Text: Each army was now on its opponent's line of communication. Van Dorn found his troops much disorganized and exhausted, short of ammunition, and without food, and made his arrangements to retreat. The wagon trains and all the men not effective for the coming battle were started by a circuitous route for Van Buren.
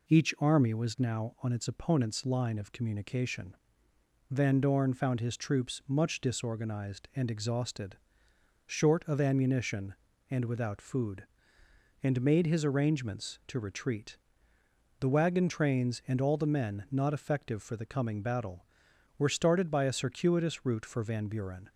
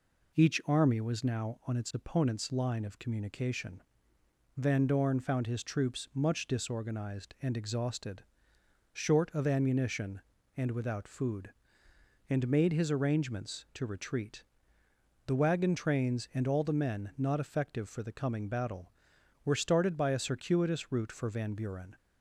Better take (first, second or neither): neither